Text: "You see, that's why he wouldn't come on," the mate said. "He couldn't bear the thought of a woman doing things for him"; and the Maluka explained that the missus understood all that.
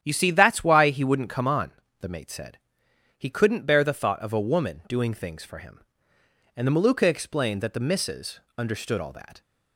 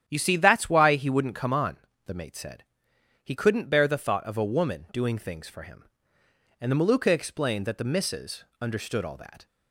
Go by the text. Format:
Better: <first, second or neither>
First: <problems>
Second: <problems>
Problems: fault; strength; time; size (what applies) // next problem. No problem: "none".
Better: neither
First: starts louder than the rest; strong; until 1.0 s; 10 dB // pauses between "missus" and "understood"; slight; at 8.3 s; 0.18 s long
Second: starts louder than the rest; strong; until 1.0 s; 10 dB // pauses between "missus" and "understood"; slight; at 8.4 s; 0.17 s long